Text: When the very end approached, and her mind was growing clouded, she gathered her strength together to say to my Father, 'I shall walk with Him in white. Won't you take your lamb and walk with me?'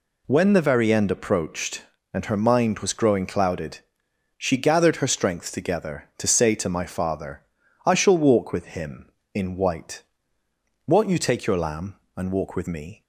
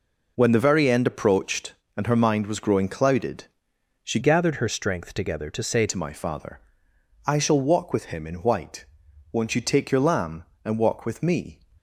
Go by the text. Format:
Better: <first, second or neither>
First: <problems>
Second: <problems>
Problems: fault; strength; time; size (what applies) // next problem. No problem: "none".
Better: first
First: none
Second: changes voice from "gathered" to "say"; from 4.2 to 5.8 s; 1.6 s long